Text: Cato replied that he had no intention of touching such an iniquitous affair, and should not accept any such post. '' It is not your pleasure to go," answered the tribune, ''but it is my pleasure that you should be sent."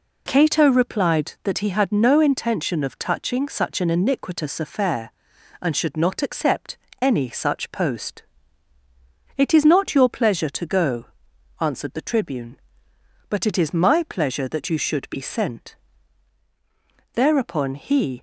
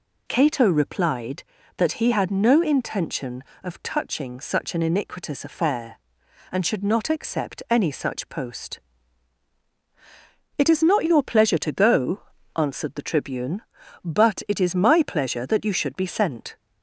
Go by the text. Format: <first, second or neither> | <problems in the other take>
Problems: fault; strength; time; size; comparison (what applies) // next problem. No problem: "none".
second | pauses between "accept" and "any"; slight; at 6.7 s; 0.24 s long // goes on to say "Thereupon he"; noticeable; from 17.1 s on; 1.0 s long